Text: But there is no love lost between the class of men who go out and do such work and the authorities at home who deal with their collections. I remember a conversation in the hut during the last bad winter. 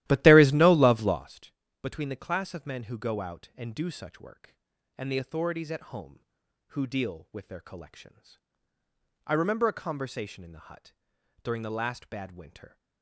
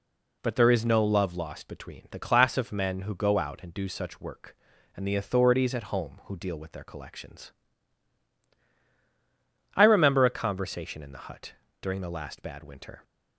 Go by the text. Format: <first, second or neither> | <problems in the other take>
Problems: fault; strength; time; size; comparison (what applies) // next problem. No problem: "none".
second | starts louder than the rest; strong; until 1.3 s; 14.5 dB // pauses between "lost" and "between"; slight; at 1.5 s; 0.30 s long // pauses between "hut" and "during"; noticeable; at 10.9 s; 0.50 s long; slight in the second